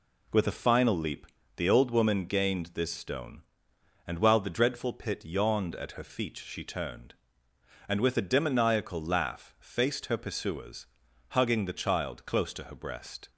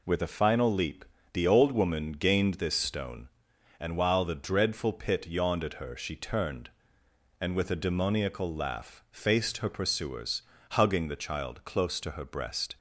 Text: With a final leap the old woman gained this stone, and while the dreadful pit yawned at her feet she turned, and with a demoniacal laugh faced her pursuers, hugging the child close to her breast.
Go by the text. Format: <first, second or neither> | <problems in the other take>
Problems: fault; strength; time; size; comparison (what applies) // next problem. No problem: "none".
first | pauses between "leap" and "the"; slight; at 1.0 s; 0.26 s long; slight in the first // skips "feet"; at 5.9 s